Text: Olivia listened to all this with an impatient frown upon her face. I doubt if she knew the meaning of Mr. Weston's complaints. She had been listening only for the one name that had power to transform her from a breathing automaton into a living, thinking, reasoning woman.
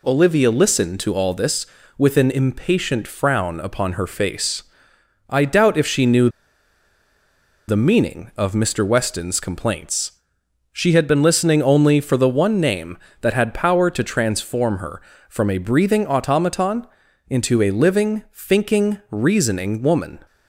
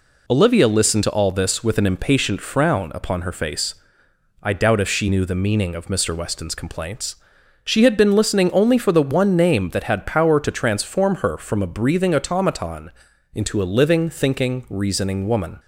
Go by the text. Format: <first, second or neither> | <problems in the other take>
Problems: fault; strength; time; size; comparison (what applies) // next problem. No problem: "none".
second | pauses between "knew" and "the"; strong; at 6.2 s; 1.3 s long // pauses between "automaton" and "into"; at 16.8 s; 0.42 s long; also in the second